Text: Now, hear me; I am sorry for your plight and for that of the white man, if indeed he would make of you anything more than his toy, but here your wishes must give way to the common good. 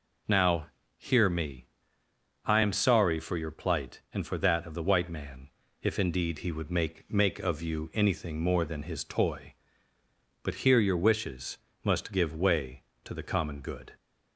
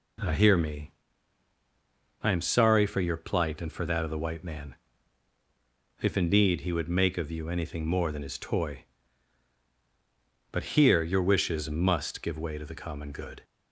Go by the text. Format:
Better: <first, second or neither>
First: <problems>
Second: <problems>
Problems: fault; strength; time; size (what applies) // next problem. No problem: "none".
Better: second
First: says "make" twice; at 7.1 s // pauses between "wishes" and "must"; slight; at 11.5 s; 0.26 s long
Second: none